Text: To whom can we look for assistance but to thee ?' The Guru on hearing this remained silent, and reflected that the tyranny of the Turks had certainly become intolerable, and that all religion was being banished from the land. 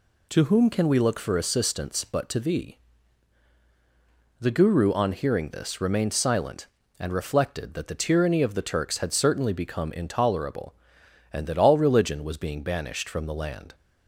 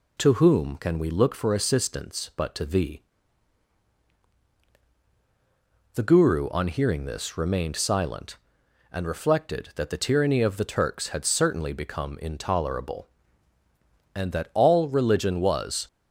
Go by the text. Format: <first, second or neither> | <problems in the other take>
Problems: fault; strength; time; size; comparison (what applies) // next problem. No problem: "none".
first | stops before "being banished from the land"; at 15.8 s